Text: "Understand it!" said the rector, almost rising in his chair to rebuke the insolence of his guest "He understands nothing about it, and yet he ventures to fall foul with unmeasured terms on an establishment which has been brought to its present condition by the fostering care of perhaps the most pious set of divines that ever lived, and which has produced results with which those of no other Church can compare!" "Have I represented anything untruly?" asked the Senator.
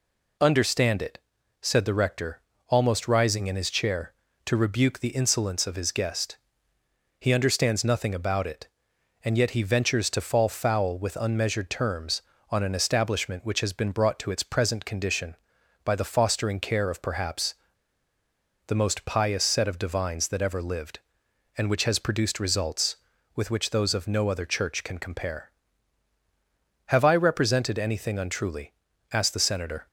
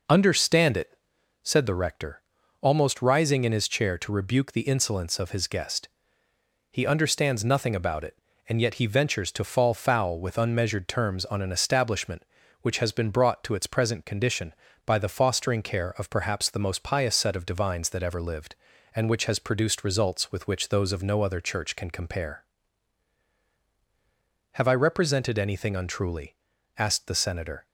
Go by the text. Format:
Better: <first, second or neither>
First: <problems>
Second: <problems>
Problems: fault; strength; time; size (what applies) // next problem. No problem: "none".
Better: second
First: pauses between "guest" and "He"; noticeable; at 6.3 s; 0.82 s long // pauses between "perhaps" and "the"; at 17.5 s; 1.1 s long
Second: pauses between "guest" and "He"; noticeable; at 5.8 s; 0.82 s long